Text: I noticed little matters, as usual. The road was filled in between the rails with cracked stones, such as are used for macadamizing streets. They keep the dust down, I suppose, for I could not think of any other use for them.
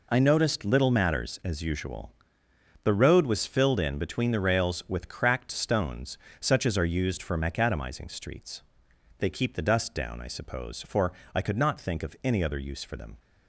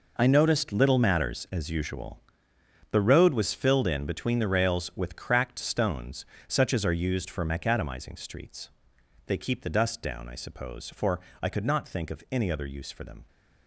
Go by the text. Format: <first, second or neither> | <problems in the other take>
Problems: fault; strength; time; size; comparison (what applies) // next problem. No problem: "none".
first | gets quieter; strong; throughout; 12.5 dB // pauses between "for" and "I"; slight; at 11.1 s; 0.24 s long; slight in the first